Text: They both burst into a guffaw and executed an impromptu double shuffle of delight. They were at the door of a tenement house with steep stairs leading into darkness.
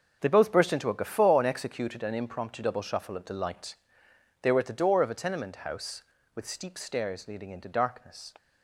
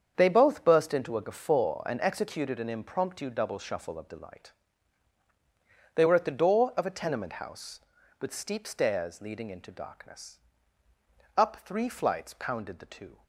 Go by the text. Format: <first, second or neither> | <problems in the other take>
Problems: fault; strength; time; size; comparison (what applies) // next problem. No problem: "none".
first | starts louder than the rest; strong; until 1.1 s; 7.5 dB; also in the first // goes on to say "Up three flights pounded the two"; strong; from 11.3 s on; 1.8 s long